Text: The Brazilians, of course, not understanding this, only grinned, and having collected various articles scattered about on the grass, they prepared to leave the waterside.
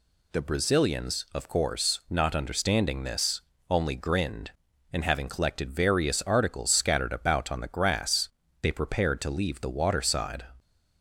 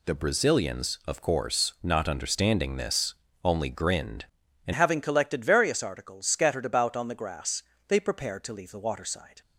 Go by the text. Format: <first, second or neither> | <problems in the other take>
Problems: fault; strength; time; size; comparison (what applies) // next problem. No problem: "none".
first | changes voice at "having"; from 4.7 s on; 4.7 s long